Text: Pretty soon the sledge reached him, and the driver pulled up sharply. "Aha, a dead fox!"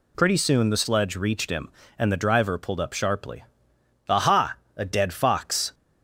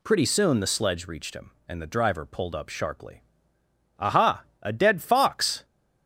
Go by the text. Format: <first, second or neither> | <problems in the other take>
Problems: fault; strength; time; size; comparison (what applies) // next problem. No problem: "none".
neither | none